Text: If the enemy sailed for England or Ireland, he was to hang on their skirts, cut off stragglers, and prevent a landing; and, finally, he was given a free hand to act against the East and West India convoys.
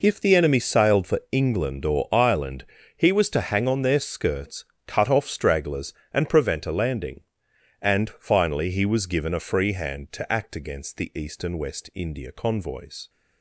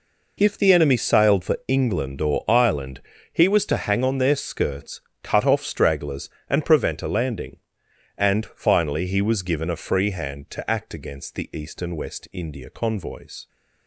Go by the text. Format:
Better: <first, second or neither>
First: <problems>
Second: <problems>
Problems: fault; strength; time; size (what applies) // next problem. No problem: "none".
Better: neither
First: none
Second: none